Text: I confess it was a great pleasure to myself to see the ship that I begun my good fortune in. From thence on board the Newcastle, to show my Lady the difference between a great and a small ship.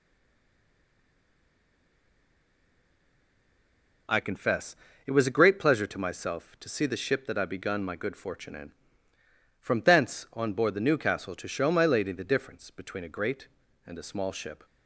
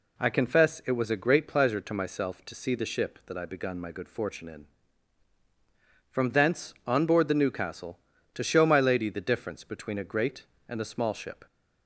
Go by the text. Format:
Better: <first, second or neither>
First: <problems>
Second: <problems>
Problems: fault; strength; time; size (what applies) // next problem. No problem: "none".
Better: second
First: stays silent before the first word; strong; until 4.0 s; 4.0 s long // pauses between "confess" and "it"; slight; at 4.7 s; 0.32 s long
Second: none